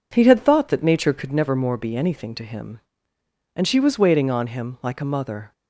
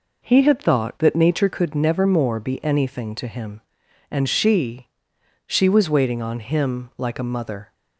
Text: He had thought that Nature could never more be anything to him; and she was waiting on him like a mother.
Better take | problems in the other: first | says "she" twice; at 5.4 s

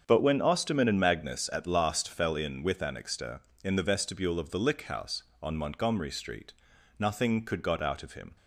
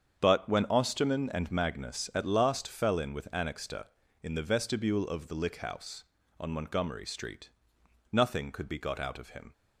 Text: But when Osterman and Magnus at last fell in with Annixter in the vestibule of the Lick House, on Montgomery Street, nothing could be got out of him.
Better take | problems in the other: second | starts louder than the rest; until 1.0 s; 7 dB; strong in the second // skips "be"; at 7.6 s

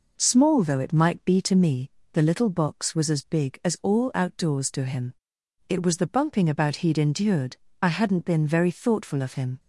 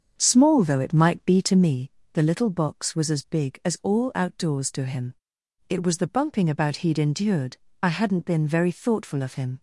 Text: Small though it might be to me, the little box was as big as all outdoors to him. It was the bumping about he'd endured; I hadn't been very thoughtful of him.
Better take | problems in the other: first | starts louder than the rest; until 1.8 s; 7 dB

